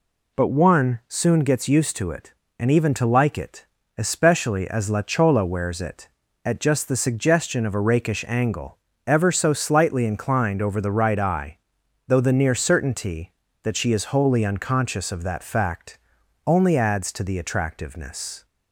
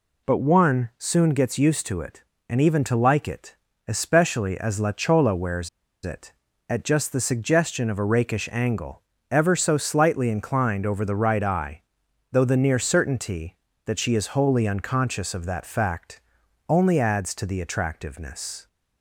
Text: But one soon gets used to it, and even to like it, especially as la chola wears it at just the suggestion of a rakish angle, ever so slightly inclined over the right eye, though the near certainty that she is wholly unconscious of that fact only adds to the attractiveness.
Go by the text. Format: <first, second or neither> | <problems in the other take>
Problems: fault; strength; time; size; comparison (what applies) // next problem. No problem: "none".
first | pauses between "wears" and "it"; at 5.6 s; 0.36 s long // pauses between "fact" and "only"; noticeable; at 16.1 s; 0.48 s long; noticeable in the first